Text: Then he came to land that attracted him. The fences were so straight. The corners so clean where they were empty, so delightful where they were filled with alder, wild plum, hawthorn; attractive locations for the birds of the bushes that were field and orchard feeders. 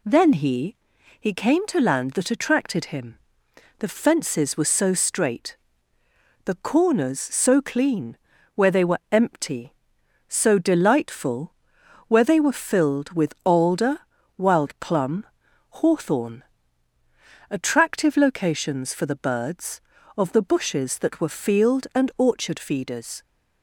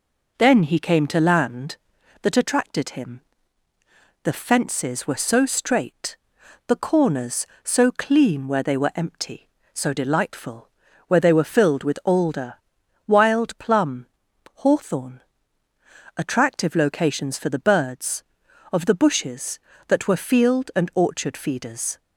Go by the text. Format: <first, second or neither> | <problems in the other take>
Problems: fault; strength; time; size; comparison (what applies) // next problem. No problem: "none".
second | says "he" twice; at 1.1 s // pauses between "clean" and "where"; at 8.1 s; 0.40 s long // pauses between "delightful" and "where"; noticeable; at 11.5 s; 0.56 s long; also in the second